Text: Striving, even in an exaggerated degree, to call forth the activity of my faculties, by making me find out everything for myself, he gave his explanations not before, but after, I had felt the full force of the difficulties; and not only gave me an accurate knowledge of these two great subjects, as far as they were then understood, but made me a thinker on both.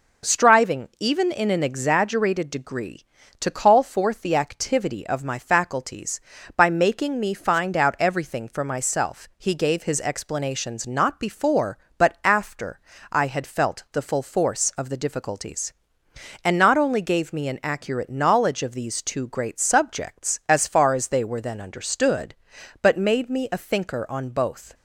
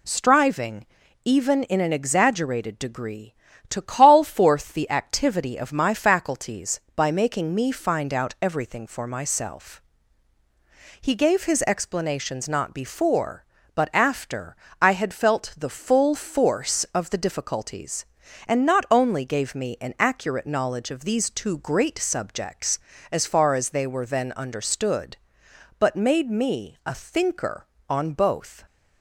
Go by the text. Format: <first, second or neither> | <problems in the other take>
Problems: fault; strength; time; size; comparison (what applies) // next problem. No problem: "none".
neither | none